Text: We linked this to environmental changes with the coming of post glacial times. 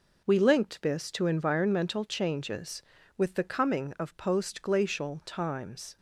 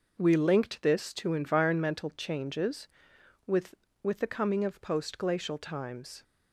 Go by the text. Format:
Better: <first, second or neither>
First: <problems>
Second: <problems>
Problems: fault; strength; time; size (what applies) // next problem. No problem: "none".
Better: first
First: none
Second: says "with" twice; at 4.0 s